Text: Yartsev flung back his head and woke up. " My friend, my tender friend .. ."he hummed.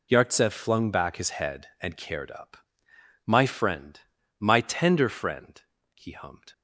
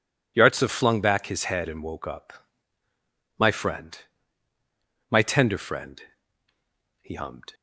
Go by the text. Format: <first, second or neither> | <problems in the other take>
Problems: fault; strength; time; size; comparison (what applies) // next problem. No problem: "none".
second | says "cared" for "woke"; at 1.9 s